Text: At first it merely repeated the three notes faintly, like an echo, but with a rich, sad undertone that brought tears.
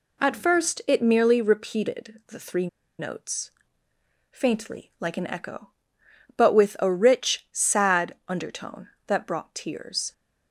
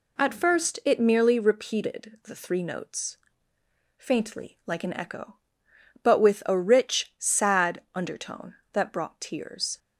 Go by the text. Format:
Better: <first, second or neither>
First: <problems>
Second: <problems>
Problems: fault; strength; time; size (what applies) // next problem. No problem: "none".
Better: second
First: pauses between "three" and "notes"; slight; at 2.6 s; 0.31 s long // pauses between "notes" and "faintly"; noticeable; at 3.5 s; 0.80 s long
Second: pauses between "notes" and "faintly"; noticeable; at 3.1 s; 0.80 s long